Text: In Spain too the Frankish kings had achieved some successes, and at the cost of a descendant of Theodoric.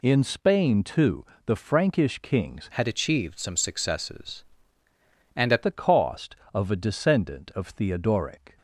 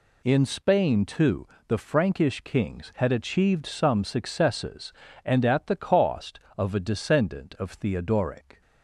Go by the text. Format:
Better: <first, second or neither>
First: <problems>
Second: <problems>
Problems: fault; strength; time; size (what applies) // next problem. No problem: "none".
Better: second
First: pauses between "too" and "the"; slight; at 1.2 s; 0.22 s long // changes voice from "had" to "at"; from 2.7 to 5.6 s; 2.9 s long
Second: pauses between "too" and "the"; slight; at 1.4 s; 0.22 s long